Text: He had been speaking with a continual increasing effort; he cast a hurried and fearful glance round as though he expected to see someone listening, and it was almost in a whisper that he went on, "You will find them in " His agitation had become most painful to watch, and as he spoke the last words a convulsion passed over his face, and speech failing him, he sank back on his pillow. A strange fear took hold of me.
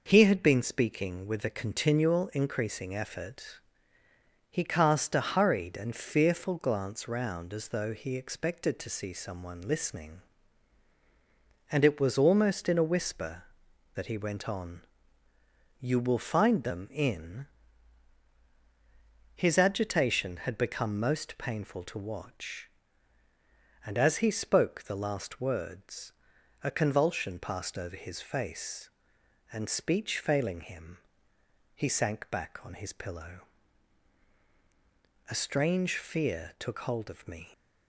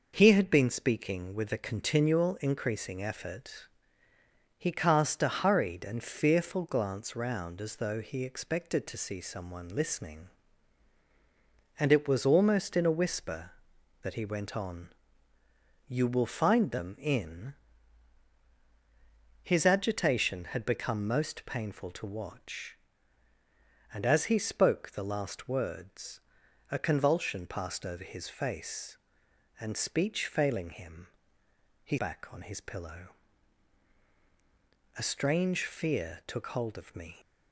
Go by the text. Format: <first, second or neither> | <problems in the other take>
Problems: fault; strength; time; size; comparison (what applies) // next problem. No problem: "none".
first | pauses between "words" and "a"; noticeable; at 26.2 s; 0.50 s long; noticeable in the first // skips "sank"; at 31.9 s